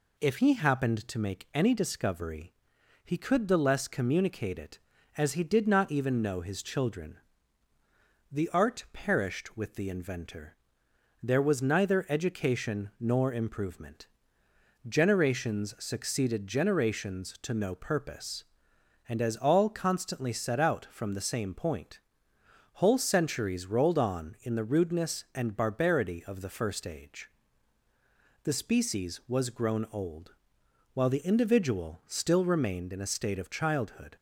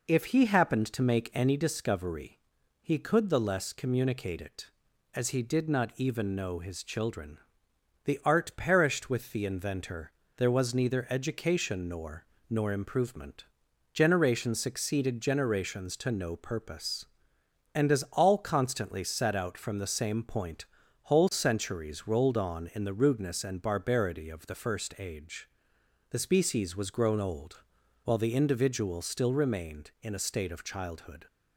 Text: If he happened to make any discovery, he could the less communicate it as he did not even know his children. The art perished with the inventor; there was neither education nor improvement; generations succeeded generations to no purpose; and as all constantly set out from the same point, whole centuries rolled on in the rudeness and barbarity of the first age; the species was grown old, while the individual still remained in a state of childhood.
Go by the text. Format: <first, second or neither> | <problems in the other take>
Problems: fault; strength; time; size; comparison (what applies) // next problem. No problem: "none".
first | says "nor" twice; at 12.4 s